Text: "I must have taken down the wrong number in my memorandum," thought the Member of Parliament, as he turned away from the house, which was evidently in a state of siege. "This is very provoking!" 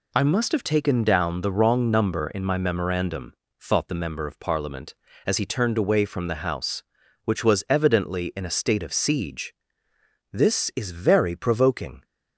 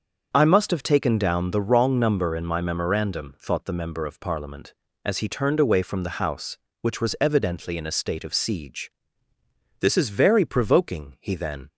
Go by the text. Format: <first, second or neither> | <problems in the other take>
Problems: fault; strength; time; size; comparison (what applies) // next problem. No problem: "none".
first | starts louder than the rest; until 1.3 s; 6.5 dB // goes on to say "He then"; from 11.1 s on; 0.50 s long